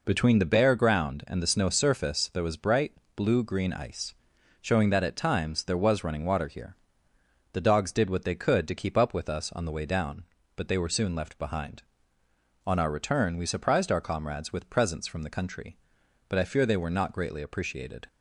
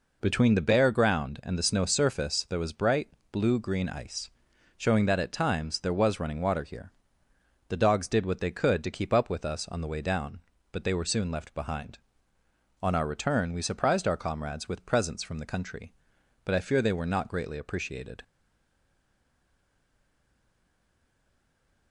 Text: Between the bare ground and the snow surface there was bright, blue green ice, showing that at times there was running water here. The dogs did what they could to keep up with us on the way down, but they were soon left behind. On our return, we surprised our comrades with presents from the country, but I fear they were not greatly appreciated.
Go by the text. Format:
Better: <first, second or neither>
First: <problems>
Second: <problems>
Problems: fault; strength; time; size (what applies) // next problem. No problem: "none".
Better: first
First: none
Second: stays silent after the last word; strong; from 18.2 s on; 3.7 s long